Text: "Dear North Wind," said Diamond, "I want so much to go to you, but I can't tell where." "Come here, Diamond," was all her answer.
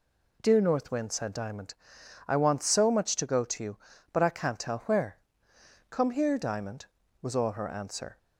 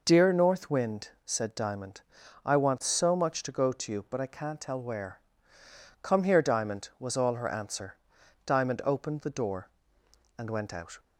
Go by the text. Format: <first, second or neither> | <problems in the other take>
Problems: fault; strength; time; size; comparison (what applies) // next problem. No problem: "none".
first | goes on to say "Diamond opened the door and went out"; strong; from 8.4 s on; 2.5 s long